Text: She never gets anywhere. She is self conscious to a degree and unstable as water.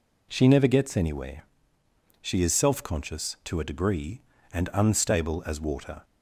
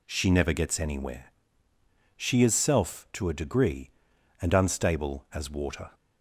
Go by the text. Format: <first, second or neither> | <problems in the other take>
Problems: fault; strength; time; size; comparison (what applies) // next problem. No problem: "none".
first | skips "conscious"; at 3.0 s